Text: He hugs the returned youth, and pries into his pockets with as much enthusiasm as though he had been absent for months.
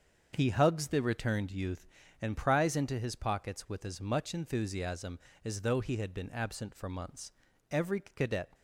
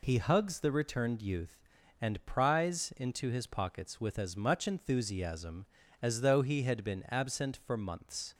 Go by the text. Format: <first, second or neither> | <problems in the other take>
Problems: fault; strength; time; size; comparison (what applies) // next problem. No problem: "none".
second | starts louder than the rest; until 1.3 s; 7 dB // goes on to say "Every cadet"; noticeable; from 7.6 s on; 0.82 s long